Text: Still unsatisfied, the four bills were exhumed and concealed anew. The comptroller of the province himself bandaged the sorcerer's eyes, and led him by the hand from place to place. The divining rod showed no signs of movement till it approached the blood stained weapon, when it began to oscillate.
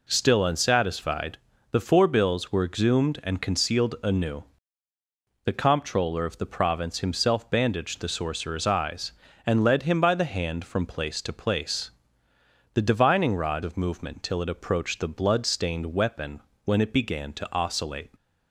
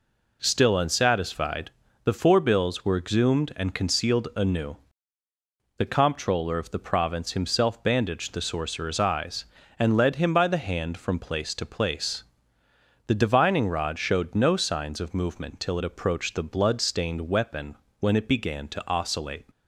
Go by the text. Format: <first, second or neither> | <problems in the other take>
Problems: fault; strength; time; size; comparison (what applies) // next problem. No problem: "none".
second | skips "showed no signs"; at 13.6 s